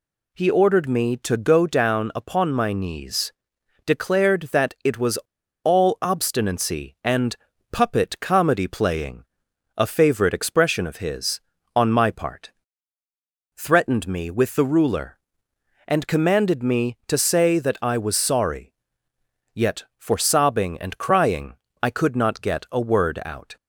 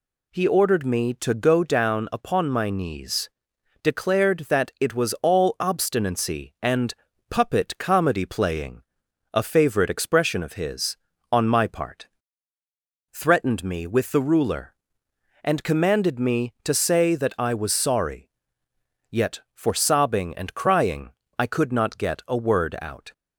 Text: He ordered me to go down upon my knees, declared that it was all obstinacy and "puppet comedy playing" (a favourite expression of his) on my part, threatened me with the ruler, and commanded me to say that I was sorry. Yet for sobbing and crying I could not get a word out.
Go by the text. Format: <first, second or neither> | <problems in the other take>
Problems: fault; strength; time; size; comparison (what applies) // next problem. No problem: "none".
second | pauses between "was" and "all"; noticeable; at 5.1 s; 0.46 s long // pauses between "and" and "puppet"; slight; at 7.3 s; 0.36 s long; slight in the second // pauses between "crying" and "I"; slight; at 21.5 s; 0.26 s long; slight in the second